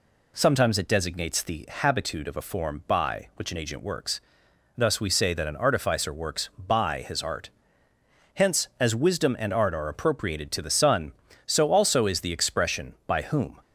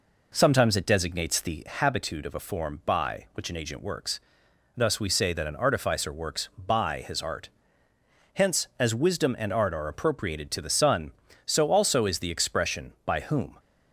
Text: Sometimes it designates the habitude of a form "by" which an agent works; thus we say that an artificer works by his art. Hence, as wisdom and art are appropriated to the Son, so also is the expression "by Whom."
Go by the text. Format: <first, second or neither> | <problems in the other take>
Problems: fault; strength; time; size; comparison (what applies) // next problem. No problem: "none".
first | starts louder than the rest; noticeable; until 1.8 s; 4 dB